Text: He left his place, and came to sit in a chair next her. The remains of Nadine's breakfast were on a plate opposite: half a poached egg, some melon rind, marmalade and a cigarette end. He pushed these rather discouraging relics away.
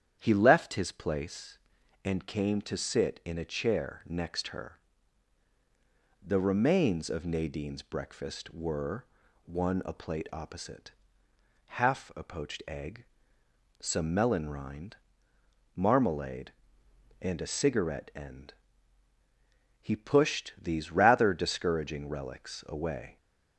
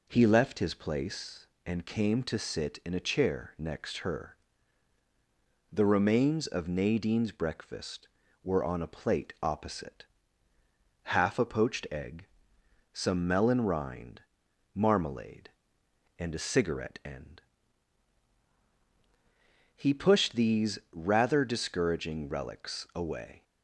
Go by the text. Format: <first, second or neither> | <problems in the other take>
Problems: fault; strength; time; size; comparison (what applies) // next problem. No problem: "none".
second | starts louder than the rest; strong; until 1.1 s; 9 dB // says "one" for "on"; at 9.4 s